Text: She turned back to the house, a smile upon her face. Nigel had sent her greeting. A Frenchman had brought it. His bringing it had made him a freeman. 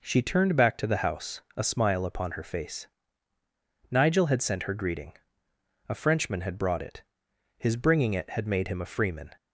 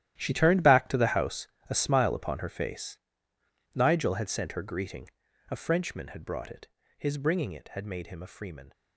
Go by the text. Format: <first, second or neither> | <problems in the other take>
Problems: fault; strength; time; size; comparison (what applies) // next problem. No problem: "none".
first | gets quieter; strong; throughout; 15.5 dB